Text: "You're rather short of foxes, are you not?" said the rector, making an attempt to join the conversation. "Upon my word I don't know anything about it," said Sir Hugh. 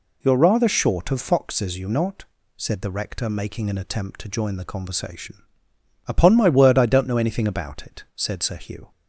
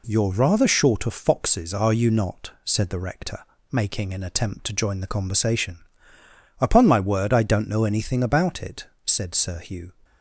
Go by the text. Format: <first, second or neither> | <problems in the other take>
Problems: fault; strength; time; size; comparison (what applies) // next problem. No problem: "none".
second | skips "are"; at 1.7 s